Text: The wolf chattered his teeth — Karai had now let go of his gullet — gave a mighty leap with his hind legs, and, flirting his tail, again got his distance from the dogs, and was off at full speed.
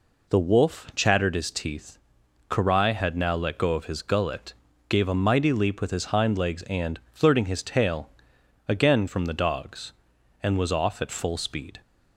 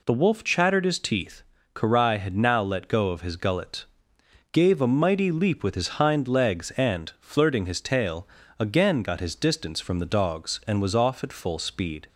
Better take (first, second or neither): second